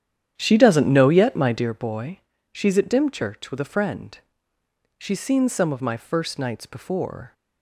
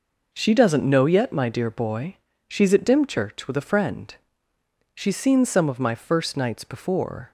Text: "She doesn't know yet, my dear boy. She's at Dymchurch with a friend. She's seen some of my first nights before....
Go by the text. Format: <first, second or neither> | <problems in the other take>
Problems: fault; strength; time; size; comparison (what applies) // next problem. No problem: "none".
second | starts louder than the rest; strong; until 1.7 s; 9.5 dB